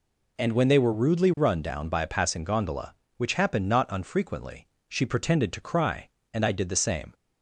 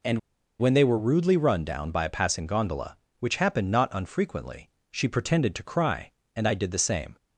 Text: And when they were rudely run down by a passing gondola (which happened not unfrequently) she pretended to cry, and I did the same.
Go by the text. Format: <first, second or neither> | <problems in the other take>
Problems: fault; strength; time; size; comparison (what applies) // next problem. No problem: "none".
first | pauses between "And" and "when"; at 0.1 s; 0.40 s long